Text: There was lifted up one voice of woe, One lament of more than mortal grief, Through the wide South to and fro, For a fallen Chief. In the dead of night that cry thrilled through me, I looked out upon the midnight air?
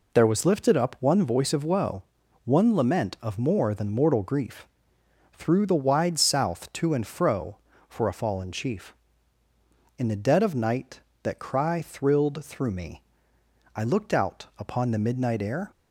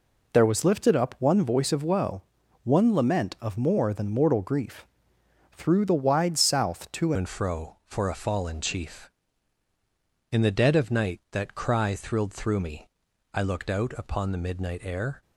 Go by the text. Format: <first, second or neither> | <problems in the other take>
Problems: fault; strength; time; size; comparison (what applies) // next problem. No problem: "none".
first | changes voice at "and"; from 7.1 s on; 8.1 s long